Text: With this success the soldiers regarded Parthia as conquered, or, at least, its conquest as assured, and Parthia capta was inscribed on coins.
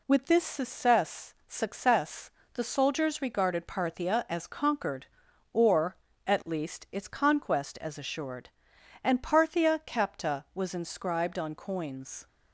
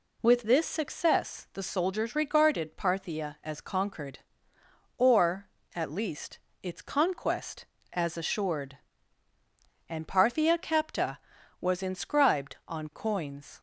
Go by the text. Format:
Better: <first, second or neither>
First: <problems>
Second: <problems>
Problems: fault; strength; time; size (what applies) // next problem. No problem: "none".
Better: second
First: says "success" twice; at 1.4 s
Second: none